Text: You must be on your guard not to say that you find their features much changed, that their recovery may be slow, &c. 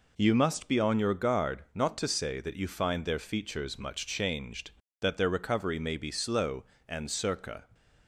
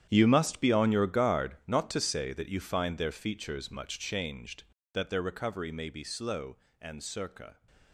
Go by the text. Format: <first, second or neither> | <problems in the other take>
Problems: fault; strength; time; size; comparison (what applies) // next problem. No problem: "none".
first | gets quieter; strong; throughout; 14 dB